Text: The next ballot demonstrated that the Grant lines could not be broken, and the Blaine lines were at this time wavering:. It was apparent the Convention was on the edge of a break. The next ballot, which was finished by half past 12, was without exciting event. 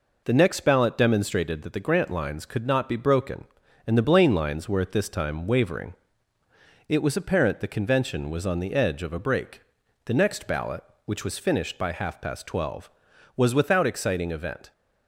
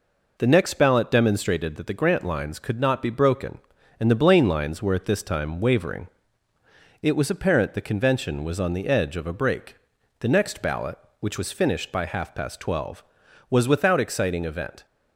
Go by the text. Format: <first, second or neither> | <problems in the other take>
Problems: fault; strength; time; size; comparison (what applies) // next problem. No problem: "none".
neither | none